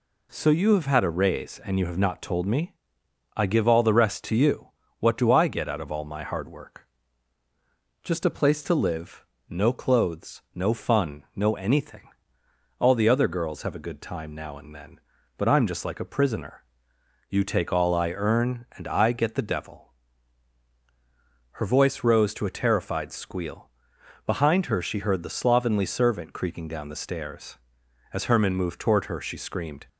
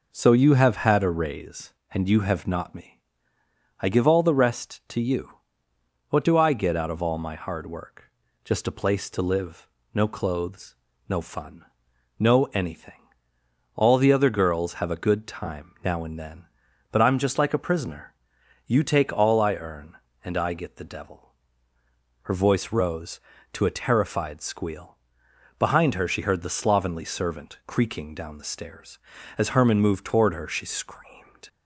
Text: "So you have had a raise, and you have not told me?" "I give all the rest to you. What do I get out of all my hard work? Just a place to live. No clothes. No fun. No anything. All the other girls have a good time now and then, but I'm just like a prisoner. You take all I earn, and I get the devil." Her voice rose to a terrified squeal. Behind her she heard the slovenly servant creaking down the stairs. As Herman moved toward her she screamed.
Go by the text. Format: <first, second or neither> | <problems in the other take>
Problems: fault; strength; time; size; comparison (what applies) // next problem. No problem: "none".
first | skips "told"; at 2.7 s